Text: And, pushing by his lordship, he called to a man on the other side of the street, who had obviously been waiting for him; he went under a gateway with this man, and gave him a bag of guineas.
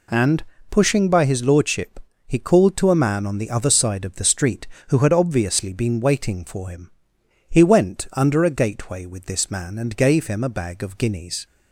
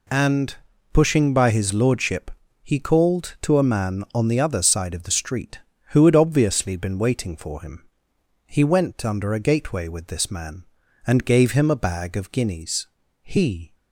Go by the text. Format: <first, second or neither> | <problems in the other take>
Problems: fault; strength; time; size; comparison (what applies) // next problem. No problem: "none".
first | goes on to say "He"; from 13.2 s on; 0.52 s long